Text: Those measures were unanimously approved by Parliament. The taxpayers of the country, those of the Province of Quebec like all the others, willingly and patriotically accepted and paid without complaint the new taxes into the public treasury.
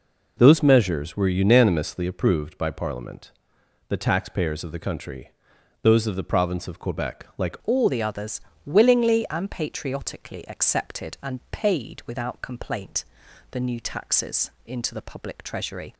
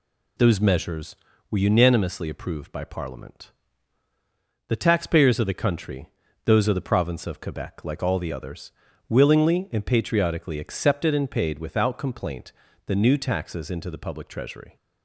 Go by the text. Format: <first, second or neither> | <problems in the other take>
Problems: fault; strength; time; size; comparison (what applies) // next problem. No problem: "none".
second | changes voice at "all"; from 7.6 s on; 8.3 s long // pauses between "complaint" and "the"; noticeable; at 13.0 s; 0.48 s long; slight in the second // pauses between "taxes" and "into"; slight; at 14.4 s; 0.16 s long